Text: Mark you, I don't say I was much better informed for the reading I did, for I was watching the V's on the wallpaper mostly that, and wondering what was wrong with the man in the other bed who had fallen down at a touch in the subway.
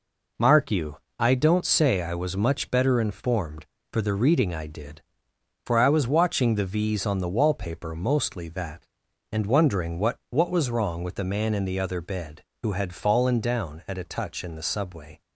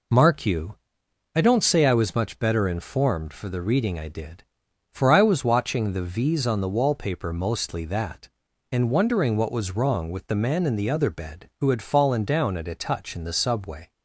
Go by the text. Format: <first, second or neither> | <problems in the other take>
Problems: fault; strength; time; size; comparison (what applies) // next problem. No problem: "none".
second | says "what" twice; at 10.3 s